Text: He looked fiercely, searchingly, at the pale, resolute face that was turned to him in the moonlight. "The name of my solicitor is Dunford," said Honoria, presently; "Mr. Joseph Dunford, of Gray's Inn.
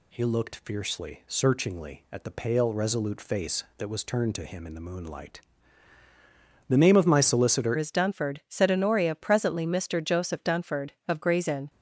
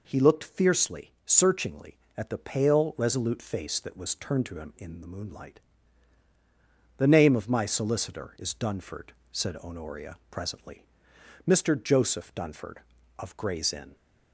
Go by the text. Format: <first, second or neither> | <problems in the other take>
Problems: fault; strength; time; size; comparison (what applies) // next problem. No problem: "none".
second | changes voice at "is"; from 7.7 s on; 3.9 s long